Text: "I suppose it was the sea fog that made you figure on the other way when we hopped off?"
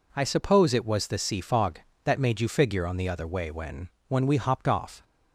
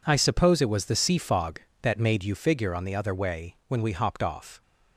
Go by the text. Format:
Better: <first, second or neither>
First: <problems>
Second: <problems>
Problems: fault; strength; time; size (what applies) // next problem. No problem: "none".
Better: second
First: says "when" twice; at 4.0 s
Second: none